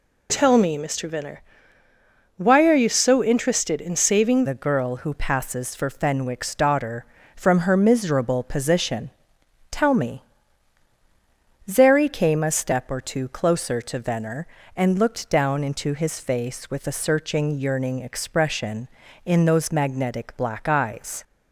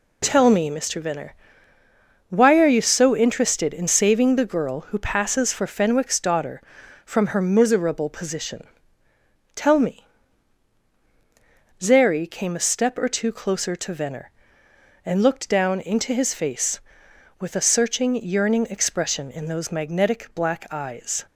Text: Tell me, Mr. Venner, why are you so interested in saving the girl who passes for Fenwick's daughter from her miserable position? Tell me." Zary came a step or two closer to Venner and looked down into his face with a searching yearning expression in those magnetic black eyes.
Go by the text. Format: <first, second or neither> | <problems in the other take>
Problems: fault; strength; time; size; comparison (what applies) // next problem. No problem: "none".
second | changes voice at "the"; from 4.4 s on; 16.8 s long